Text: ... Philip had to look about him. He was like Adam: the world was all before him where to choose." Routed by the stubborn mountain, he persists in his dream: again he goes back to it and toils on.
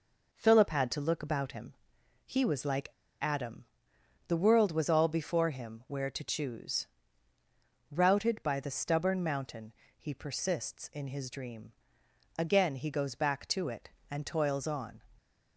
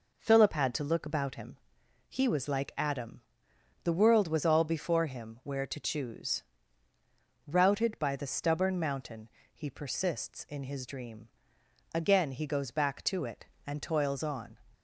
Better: second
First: pauses between "like" and "Adam"; slight; at 2.8 s; 0.33 s long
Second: none

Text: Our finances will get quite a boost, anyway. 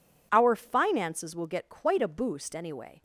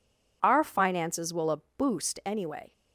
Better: first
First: none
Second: skips "get quite"; at 1.4 s // pauses between "a" and "boost"; slight; at 1.5 s; 0.18 s long

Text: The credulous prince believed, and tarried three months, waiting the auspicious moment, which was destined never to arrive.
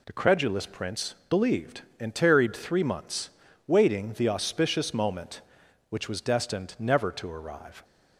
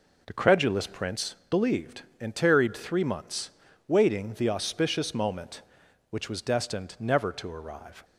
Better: first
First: pauses between "prince" and "believed"; slight; at 1.1 s; 0.16 s long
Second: starts louder than the rest; noticeable; until 1.3 s; 4.5 dB // pauses between "prince" and "believed"; slight; at 1.3 s; 0.16 s long

